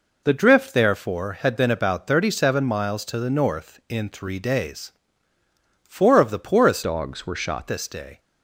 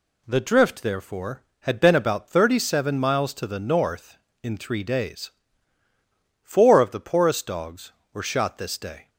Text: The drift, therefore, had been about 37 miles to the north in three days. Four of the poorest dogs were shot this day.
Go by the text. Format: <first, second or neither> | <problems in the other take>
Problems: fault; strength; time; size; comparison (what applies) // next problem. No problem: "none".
second | changes voice from "dogs" to "shot"; from 6.8 to 7.6 s; 0.8 s long